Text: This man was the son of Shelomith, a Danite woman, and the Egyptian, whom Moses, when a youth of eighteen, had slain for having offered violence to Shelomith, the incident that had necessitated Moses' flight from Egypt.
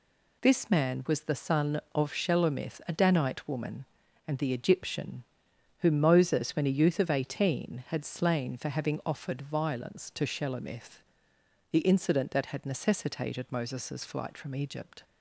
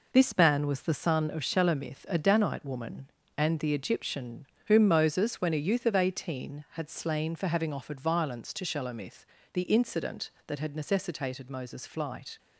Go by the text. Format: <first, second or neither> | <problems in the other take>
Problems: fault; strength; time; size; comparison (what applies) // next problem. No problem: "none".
first | stops before "from Egypt"; at 12.3 s